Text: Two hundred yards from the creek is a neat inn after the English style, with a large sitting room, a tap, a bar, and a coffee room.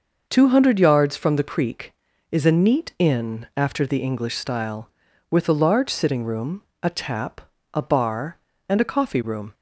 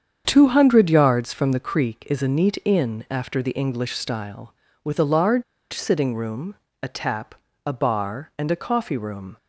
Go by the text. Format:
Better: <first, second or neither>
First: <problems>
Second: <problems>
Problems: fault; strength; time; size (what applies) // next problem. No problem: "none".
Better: first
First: none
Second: starts louder than the rest; strong; until 1.2 s; 8 dB // pauses between "large" and "sitting"; slight; at 5.4 s; 0.29 s long